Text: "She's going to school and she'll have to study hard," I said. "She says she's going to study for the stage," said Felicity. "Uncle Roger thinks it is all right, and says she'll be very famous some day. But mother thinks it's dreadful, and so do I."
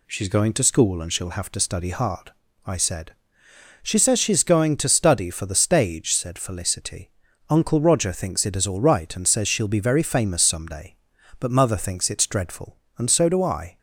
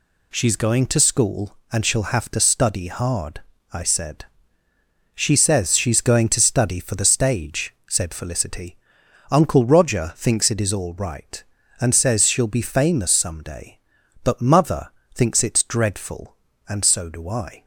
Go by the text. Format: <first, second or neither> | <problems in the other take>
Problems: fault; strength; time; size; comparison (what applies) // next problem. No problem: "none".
first | skips "very"; at 12.6 s // pauses between "mother" and "thinks"; slight; at 14.8 s; 0.24 s long